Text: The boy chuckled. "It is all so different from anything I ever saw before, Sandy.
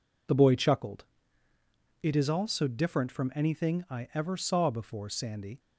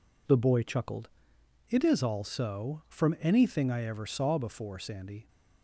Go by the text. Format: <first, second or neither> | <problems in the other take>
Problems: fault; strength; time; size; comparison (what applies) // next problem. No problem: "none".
first | skips "different"; at 2.8 s